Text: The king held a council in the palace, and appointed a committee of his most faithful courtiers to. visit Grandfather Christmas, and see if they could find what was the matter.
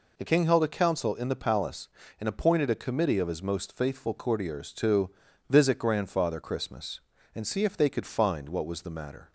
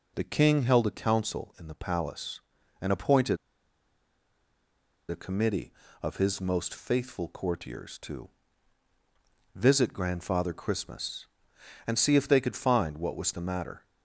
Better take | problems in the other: first | pauses between "appointed" and "a"; strong; at 3.3 s; 1.7 s long

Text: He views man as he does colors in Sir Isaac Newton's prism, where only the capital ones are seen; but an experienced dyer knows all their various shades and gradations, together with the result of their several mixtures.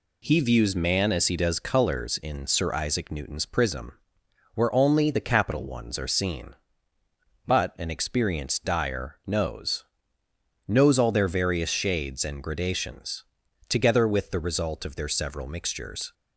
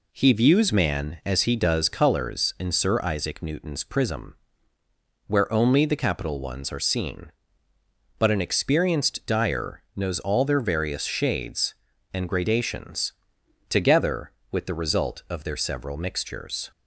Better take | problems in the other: second | says "knows" twice; at 10.6 s

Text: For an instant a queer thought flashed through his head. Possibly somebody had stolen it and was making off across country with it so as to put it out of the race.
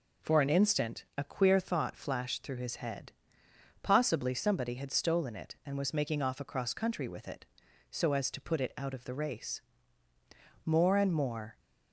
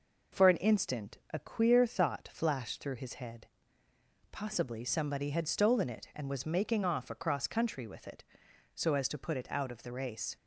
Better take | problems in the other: second | goes on to say "More and more"; noticeable; from 10.6 s on; 0.94 s long

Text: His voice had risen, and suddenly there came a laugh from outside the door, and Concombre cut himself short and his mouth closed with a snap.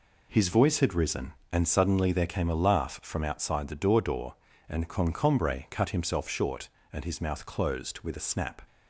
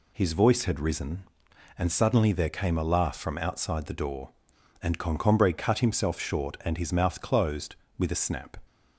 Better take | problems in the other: second | says "door" twice; at 4.0 s

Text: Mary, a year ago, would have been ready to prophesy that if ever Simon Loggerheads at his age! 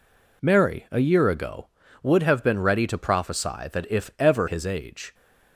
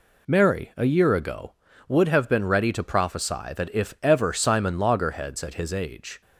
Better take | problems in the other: second | skips "Simon Loggerheads at"; at 4.4 s

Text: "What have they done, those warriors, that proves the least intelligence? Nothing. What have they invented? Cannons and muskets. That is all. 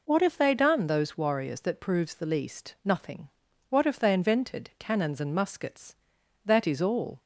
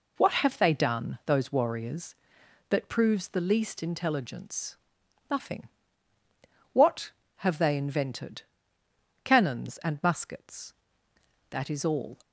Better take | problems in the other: second | skips "intelligence"; at 2.7 s

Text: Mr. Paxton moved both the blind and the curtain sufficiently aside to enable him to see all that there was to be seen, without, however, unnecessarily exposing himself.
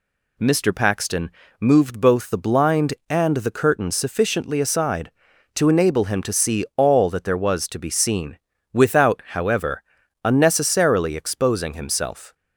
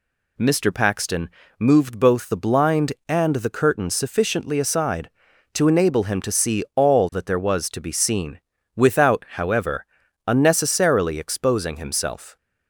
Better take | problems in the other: neither | pauses between "Paxton" and "moved"; slight; the same in both

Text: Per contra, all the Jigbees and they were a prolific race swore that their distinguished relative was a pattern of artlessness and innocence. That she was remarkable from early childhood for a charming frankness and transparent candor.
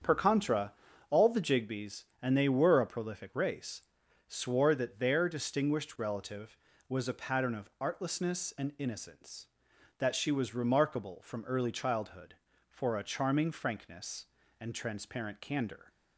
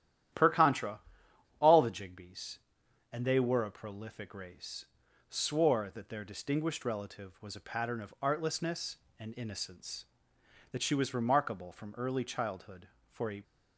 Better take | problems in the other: first | starts louder than the rest; strong; until 1.9 s; 11.5 dB; strong in the first // pauses between "race" and "swore"; noticeable; at 4.8 s; 0.46 s long; also in the first // stops before "charming frankness and transparent candor"; at 13.4 s

